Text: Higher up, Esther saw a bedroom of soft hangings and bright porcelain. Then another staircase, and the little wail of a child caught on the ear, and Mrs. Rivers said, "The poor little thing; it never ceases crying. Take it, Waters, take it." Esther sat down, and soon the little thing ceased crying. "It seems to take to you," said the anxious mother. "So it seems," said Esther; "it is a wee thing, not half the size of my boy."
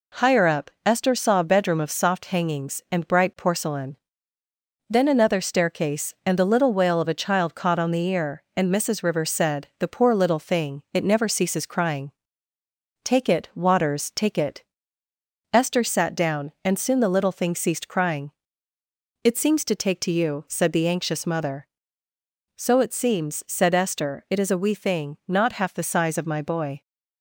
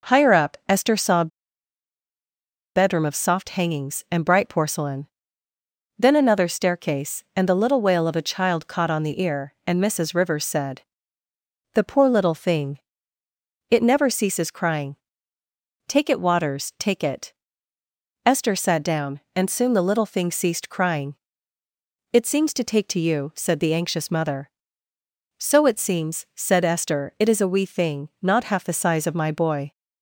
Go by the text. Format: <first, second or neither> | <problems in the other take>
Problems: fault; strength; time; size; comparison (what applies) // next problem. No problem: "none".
first | pauses between "a" and "bedroom"; strong; at 1.2 s; 1.4 s long